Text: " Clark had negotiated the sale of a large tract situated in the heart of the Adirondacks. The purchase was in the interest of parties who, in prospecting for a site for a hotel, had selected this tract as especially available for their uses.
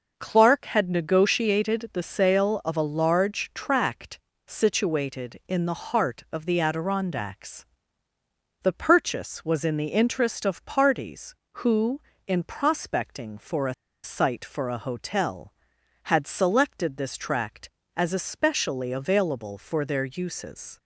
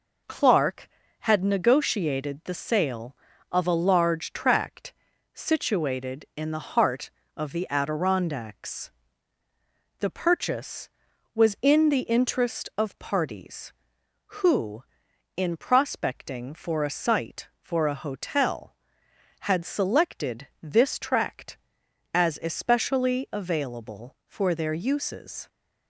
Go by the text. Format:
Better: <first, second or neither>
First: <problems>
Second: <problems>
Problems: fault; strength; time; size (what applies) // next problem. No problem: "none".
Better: second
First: pauses between "tract" and "situated"; slight; at 4.1 s; 0.30 s long // pauses between "a" and "site"; slight; at 13.7 s; 0.30 s long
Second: pauses between "tract" and "situated"; at 4.9 s; 0.40 s long